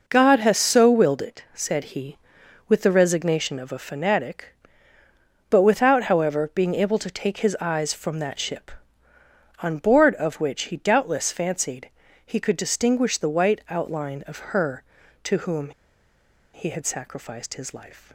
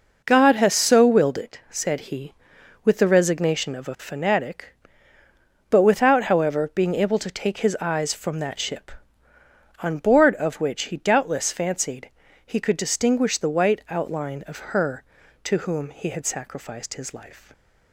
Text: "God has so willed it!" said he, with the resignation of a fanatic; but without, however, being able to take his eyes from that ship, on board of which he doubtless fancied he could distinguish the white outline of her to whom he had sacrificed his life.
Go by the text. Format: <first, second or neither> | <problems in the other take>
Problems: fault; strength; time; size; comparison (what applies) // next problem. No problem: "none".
second | pauses between "fancied" and "he"; slight; at 11.8 s; 0.36 s long; slight in the second // pauses between "whom" and "he"; noticeable; at 15.7 s; 0.83 s long